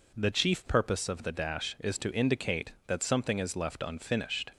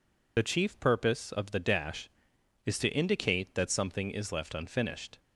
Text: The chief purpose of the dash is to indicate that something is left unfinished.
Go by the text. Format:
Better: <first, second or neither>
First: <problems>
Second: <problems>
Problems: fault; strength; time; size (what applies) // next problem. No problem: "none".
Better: first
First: none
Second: loses the start of "The"; at 0.3 s; 55 ms